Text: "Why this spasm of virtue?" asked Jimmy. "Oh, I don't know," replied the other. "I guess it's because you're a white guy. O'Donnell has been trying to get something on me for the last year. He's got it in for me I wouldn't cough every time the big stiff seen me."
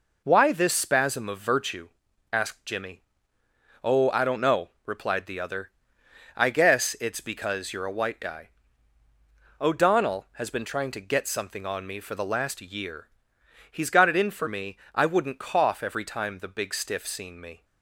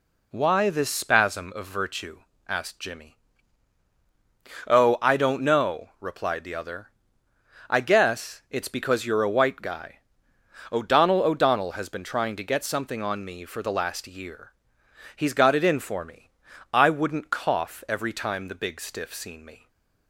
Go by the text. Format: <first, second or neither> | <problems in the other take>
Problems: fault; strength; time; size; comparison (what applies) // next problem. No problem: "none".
first | says "O'Donnell" twice; at 11.2 s // pauses between "me" and "I"; at 16.2 s; 0.42 s long; slight in the first // stays silent after the last word; slight; from 19.5 s on; 0.5 s long